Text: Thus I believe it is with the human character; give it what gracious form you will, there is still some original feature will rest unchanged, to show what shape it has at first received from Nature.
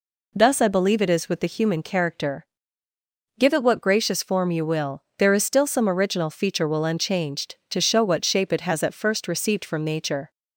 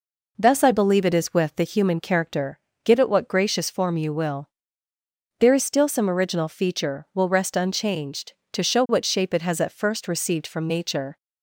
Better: second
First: skips "rest"; at 6.8 s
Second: none

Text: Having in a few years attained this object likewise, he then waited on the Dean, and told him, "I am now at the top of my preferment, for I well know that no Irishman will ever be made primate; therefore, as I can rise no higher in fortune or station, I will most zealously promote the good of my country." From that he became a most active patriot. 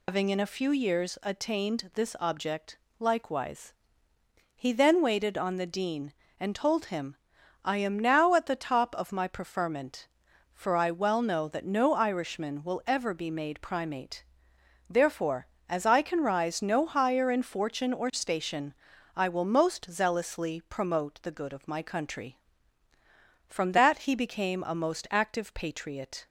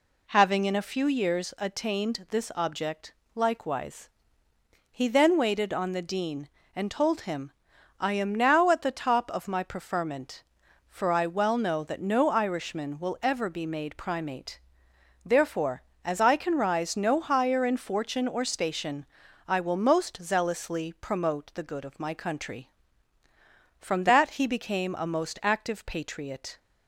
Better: second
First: loses the start of "Having"; at 0.0 s; 155 ms // pauses between "object" and "likewise"; slight; at 2.7 s; 0.22 s long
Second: pauses between "object" and "likewise"; slight; at 3.1 s; 0.22 s long

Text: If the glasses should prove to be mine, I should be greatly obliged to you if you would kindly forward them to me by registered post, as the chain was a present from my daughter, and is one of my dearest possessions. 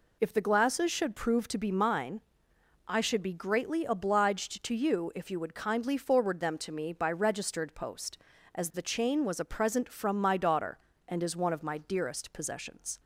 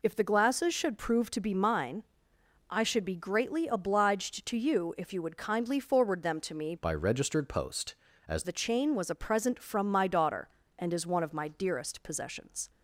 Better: first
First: none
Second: changes voice from "by" to "as"; from 6.7 to 8.4 s; 1.7 s long

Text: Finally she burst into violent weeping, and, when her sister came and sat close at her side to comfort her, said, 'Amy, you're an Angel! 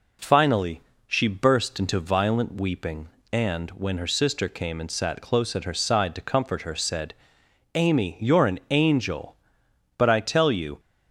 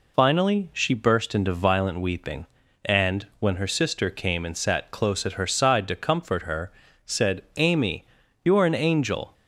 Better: second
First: pauses between "Finally" and "she"; slight; at 0.8 s; 0.26 s long // goes on to say "But I tell you"; noticeable; from 9.9 s on; 0.84 s long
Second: none

